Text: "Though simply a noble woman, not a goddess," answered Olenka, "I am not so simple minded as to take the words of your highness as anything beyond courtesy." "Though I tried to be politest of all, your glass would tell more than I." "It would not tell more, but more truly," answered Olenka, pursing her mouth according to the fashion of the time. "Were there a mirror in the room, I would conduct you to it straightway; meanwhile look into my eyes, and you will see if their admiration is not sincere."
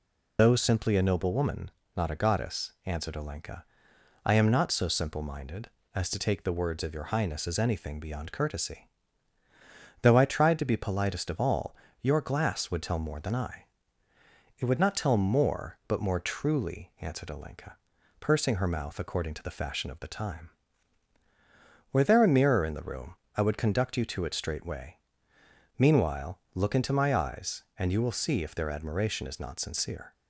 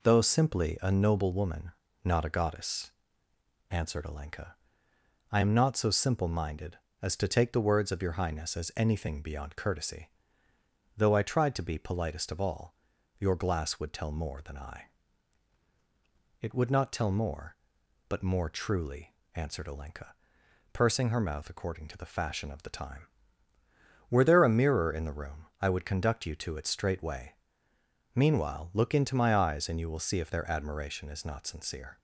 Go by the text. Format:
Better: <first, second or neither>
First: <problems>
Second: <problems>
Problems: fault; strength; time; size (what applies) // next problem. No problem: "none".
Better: second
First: loses the start of "Though"; at 0.3 s; 80 ms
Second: none